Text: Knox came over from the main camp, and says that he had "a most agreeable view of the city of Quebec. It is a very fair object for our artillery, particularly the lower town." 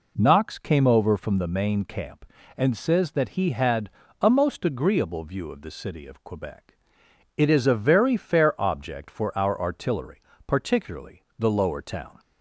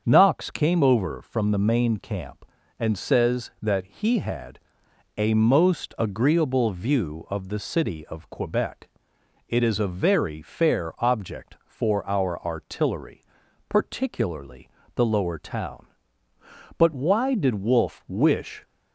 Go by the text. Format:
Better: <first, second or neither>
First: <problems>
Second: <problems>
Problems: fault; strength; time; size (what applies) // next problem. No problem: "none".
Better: first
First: pauses between "had" and "a"; slight; at 3.8 s; 0.32 s long // pauses between "particularly" and "the"; slight; at 11.2 s; 0.16 s long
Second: starts louder than the rest; strong; until 1.0 s; 7 dB // pauses between "had" and "a"; noticeable; at 4.5 s; 0.60 s long // pauses between "particularly" and "the"; slight; at 14.7 s; 0.24 s long // goes on to say "But why did Wolfe wish"; strong; from 16.7 s on; 1.8 s long